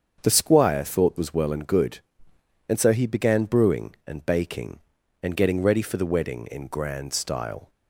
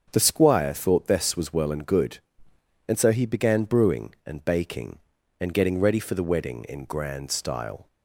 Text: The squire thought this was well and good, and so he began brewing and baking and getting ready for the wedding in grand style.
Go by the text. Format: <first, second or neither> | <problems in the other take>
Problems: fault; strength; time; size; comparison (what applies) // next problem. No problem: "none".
second | starts louder than the rest; strong; until 1.2 s; 7 dB; strong in the second // skips "this"; at 1.1 s